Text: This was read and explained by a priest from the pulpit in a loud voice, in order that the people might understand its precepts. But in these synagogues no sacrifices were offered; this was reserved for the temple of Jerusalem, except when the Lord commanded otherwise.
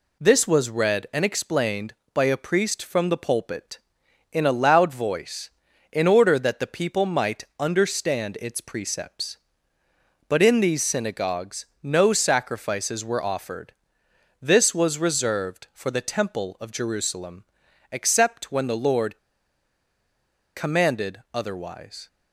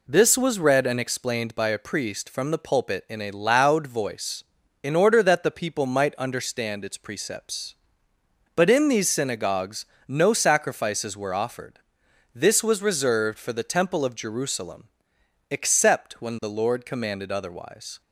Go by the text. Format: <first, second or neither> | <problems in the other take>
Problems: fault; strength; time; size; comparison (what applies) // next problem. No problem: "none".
second | pauses between "might" and "understand"; slight; at 7.4 s; 0.16 s long // pauses between "synagogues" and "no"; slight; at 11.6 s; 0.16 s long; slight in the second // pauses between "Lord" and "commanded"; strong; at 19.1 s; 1.3 s long